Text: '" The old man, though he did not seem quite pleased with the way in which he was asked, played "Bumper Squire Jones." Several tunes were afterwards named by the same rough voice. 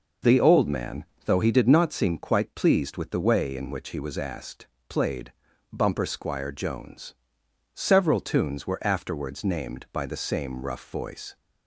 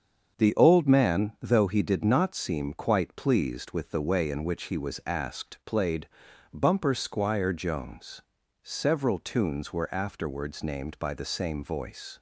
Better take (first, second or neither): first